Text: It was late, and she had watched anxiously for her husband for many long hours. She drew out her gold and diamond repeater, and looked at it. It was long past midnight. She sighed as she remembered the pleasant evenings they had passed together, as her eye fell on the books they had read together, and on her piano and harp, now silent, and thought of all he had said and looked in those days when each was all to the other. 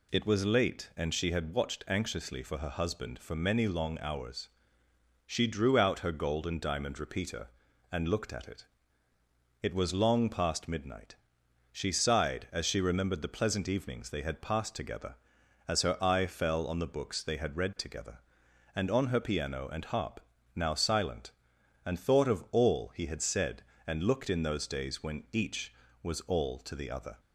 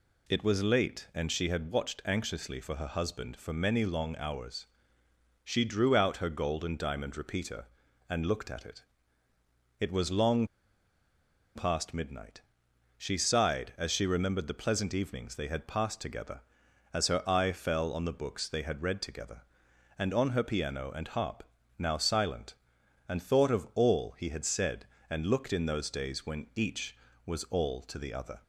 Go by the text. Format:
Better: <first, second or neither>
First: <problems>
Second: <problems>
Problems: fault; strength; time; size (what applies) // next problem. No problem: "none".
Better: first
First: none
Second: pauses between "long" and "past"; at 10.4 s; 1.1 s long